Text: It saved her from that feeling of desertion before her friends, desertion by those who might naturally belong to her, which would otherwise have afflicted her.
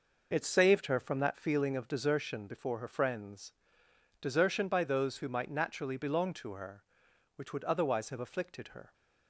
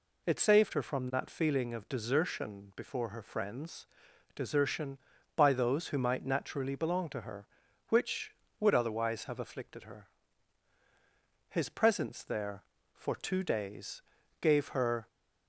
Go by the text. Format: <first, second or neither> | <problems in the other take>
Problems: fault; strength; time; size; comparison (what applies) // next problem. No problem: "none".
first | goes on to say "His presence there for two days gave her"; strong; from 11.4 s on; 3.5 s long